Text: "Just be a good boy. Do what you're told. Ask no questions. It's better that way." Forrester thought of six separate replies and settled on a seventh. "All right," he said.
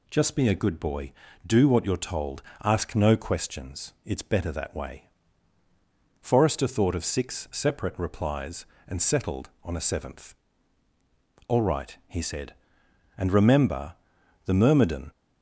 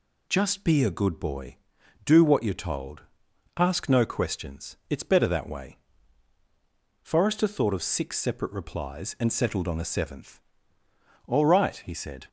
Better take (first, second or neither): second